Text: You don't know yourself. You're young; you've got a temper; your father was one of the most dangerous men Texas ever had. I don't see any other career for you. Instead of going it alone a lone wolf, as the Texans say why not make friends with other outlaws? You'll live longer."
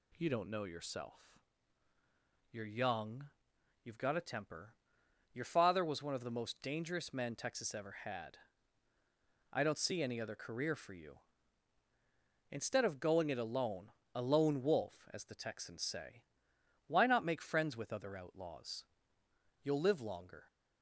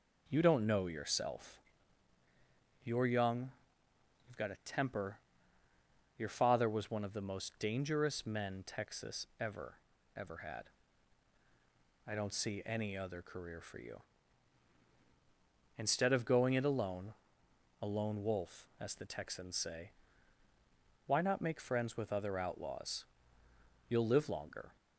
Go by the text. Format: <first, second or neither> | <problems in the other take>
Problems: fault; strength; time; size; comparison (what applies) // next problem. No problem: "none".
first | says "ever" twice; at 10.1 s // pauses between "alone" and "a"; noticeable; at 17.1 s; 0.66 s long; slight in the first // pauses between "say" and "why"; at 19.8 s; 1.1 s long; noticeable in the first